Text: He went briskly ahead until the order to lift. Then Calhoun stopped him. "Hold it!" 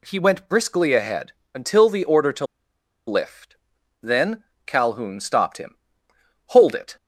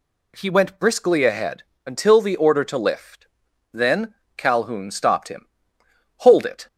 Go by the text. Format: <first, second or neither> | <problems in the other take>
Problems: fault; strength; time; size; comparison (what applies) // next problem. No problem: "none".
second | pauses between "ahead" and "until"; slight; at 1.3 s; 0.24 s long; slight in the second // pauses between "to" and "lift"; noticeable; at 2.4 s; 0.62 s long // pauses between "Then" and "Calhoun"; slight; at 4.4 s; 0.20 s long; slight in the second